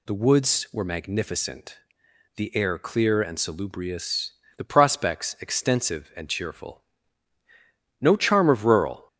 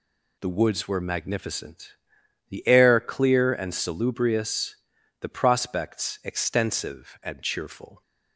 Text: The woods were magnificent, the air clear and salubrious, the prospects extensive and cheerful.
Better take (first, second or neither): second